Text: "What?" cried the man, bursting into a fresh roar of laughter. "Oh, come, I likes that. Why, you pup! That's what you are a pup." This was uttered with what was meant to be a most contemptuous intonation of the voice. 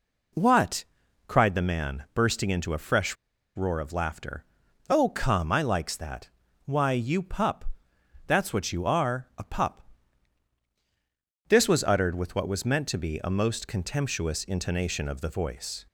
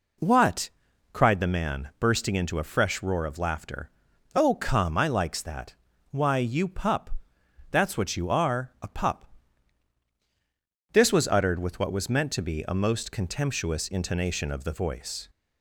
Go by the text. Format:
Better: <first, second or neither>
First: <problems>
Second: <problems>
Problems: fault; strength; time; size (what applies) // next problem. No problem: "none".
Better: second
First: pauses between "fresh" and "roar"; at 3.1 s; 0.40 s long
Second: none